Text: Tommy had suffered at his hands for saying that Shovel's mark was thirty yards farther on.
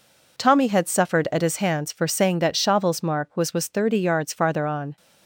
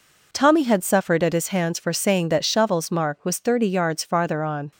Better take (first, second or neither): second